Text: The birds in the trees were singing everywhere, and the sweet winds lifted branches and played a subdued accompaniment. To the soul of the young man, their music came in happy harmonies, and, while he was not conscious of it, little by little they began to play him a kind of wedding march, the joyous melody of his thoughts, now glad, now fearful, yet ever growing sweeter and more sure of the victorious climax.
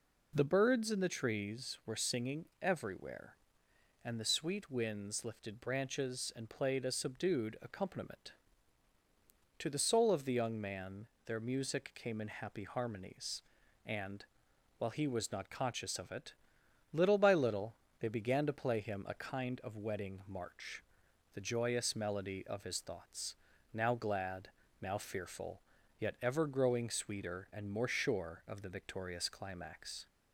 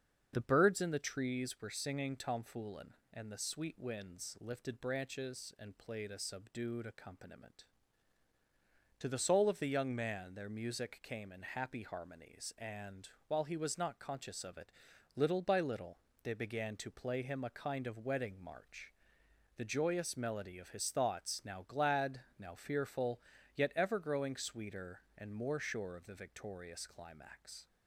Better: first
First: pauses between "little" and "they"; slight; at 17.7 s; 0.24 s long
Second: starts louder than the rest; until 1.3 s; 7 dB // says "tomfoolin" for "everywhere"; at 2.1 s // pauses between "little" and "they"; slight; at 15.9 s; 0.26 s long

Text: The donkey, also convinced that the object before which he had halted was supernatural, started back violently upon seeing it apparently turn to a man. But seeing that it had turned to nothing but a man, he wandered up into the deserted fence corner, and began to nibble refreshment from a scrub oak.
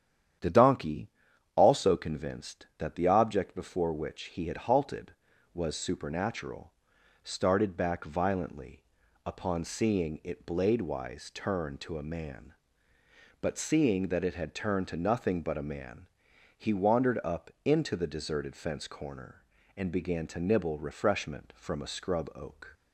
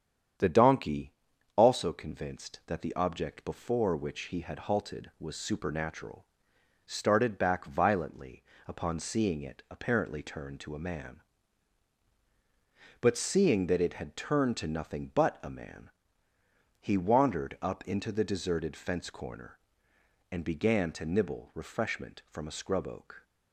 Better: second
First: starts louder than the rest; strong; until 1.8 s; 9.5 dB // pauses between "violently" and "upon"; at 8.8 s; 0.42 s long // says "bladewise" for "apparently"; at 10.4 s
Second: starts louder than the rest; strong; until 1.8 s; 8.5 dB // pauses between "violently" and "upon"; slight; at 8.4 s; 0.24 s long

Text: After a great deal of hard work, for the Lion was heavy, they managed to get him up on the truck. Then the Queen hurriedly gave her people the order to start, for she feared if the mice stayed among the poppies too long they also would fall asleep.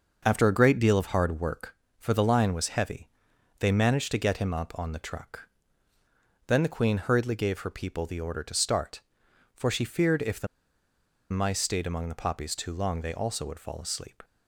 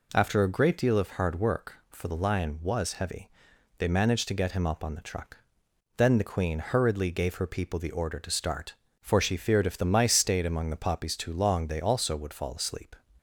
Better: second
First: starts louder than the rest; until 1.2 s; 6.5 dB // pauses between "the" and "mice"; noticeable; at 10.4 s; 0.84 s long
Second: none

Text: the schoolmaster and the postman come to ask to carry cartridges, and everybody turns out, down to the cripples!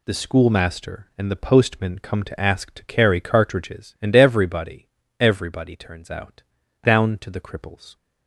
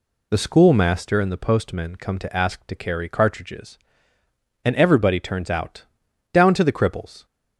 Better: second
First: says "everybody" twice; at 5.1 s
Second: none

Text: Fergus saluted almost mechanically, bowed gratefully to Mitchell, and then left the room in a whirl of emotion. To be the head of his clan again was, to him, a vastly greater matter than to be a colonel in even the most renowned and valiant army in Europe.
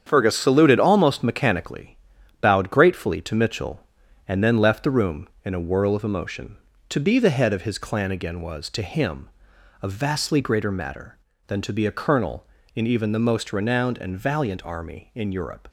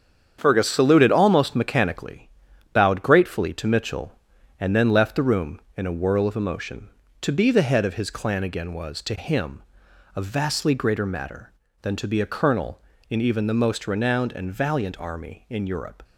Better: neither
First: starts louder than the rest; strong; until 1.0 s; 8 dB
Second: starts louder than the rest; strong; until 1.4 s; 8 dB

